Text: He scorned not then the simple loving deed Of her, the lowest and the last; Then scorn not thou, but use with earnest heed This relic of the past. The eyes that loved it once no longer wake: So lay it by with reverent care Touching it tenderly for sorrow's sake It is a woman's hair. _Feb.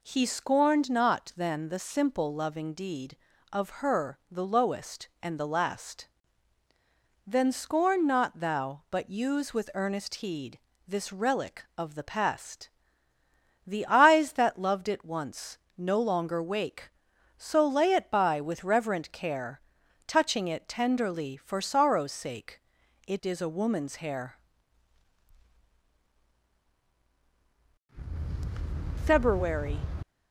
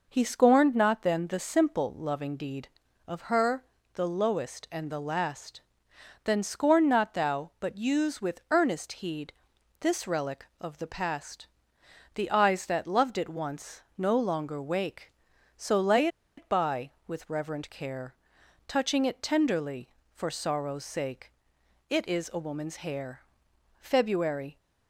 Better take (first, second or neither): first